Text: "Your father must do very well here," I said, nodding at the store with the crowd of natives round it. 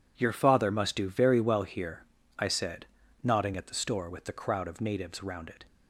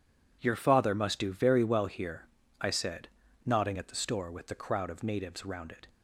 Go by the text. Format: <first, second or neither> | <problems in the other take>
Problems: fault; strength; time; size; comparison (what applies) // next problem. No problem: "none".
neither | none